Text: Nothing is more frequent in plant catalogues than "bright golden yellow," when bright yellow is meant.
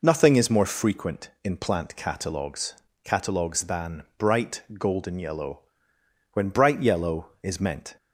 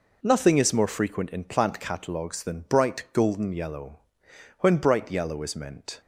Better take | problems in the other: second | says "catalogues" twice; at 3.0 s // pauses between "than" and "bright"; slight; at 4.0 s; 0.16 s long

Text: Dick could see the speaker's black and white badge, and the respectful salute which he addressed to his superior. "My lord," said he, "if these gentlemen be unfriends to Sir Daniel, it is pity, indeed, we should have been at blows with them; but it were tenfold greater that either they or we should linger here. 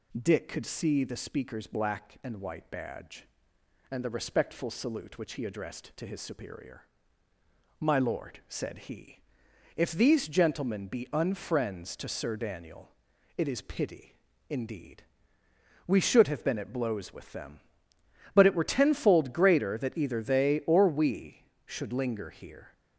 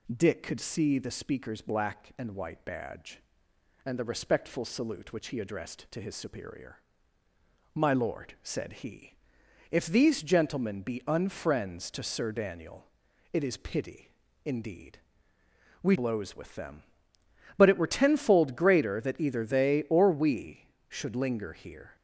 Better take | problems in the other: first | skips "should have been at"; at 15.9 s

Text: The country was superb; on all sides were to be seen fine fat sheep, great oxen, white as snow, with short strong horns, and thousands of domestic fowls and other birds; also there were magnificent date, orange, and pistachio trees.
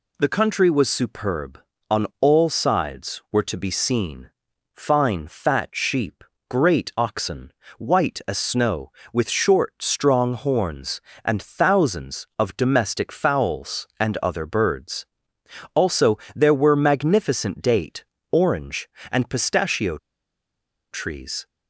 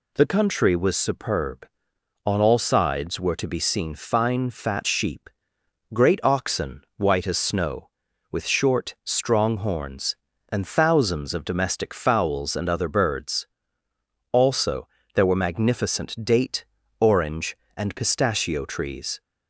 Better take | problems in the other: second | pauses between "seen" and "fine"; at 4.2 s; 0.44 s long // pauses between "also" and "there"; slight; at 16.1 s; 0.16 s long; slight in the second // pauses between "pistachio" and "trees"; noticeable; at 19.9 s; 0.94 s long

